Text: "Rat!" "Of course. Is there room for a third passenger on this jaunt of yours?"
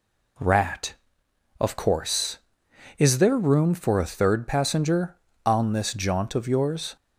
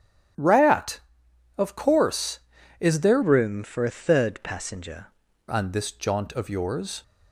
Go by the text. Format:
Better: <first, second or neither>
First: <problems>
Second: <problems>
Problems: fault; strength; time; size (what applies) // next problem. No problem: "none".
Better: first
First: none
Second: starts louder than the rest; strong; until 1.9 s; 10.5 dB // changes voice from "room" to "passenger"; from 3.2 to 5.0 s; 1.8 s long